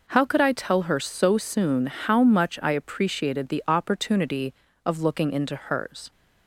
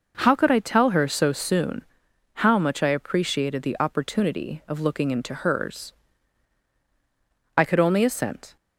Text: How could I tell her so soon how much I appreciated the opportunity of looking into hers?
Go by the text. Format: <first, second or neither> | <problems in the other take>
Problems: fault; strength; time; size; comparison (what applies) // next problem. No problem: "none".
first | pauses between "soon" and "how"; noticeable; at 1.8 s; 0.56 s long // goes on to say "I could only assent"; noticeable; from 7.5 s on; 1.0 s long